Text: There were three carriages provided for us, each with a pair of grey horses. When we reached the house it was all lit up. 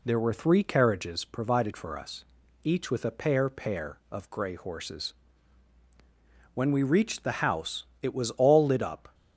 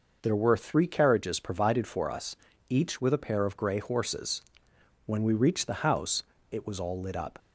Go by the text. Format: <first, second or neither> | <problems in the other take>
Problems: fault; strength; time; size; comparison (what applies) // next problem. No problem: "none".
second | says "pair" twice; at 3.4 s // pauses between "house" and "it"; slight; at 7.8 s; 0.18 s long; slight in the second